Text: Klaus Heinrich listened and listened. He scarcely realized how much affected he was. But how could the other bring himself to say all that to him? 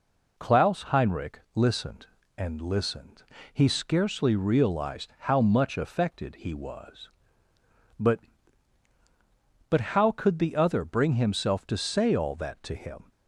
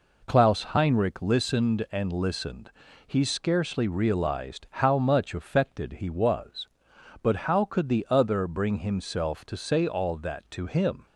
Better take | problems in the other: second | says "But" twice; at 9.6 s

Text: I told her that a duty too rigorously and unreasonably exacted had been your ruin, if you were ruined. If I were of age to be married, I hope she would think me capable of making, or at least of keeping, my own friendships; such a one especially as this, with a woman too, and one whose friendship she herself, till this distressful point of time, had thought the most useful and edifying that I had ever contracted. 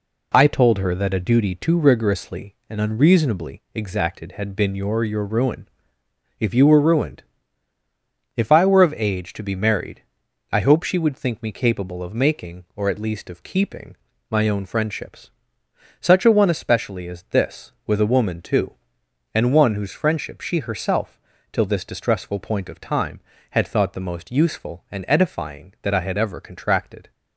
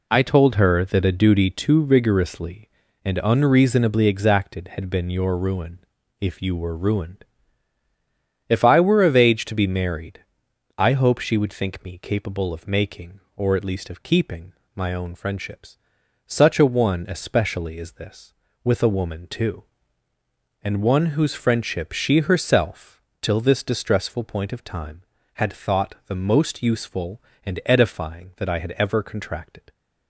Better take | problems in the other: second | says "your" twice; at 5.0 s

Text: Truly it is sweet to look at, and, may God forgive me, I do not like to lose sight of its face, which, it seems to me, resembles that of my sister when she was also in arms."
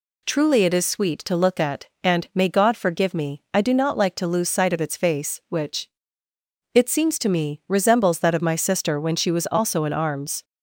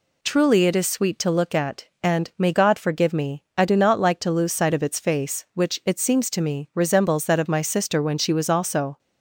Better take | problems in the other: first | stops before "in arms"; at 8.9 s

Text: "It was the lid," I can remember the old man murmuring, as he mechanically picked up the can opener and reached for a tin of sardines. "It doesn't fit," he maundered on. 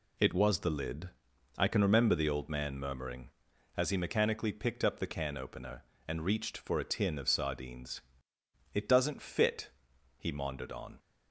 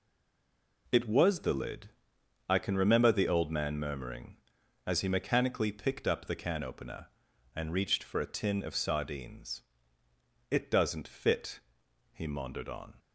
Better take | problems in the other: first | stays silent before the first word; slight; until 0.8 s; 0.8 s long

